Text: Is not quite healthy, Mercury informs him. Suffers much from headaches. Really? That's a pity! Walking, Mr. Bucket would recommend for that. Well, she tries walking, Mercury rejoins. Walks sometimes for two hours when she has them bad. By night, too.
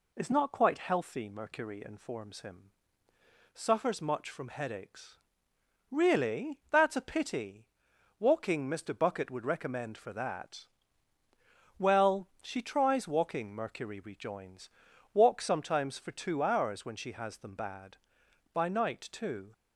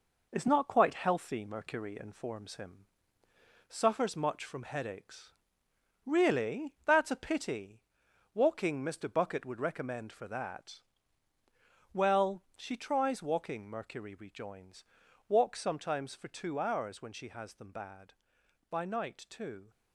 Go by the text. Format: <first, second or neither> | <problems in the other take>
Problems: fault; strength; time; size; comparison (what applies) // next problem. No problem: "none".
first | gets quieter; noticeable; throughout; 4.5 dB